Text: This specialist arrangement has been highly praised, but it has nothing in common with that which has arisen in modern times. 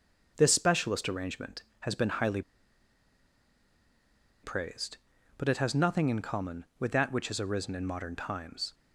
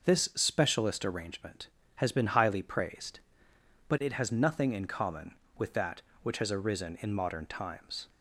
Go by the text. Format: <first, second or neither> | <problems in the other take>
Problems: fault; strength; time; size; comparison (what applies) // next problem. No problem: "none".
second | starts louder than the rest; until 1.3 s; 6.5 dB // pauses between "highly" and "praised"; strong; at 2.4 s; 2.0 s long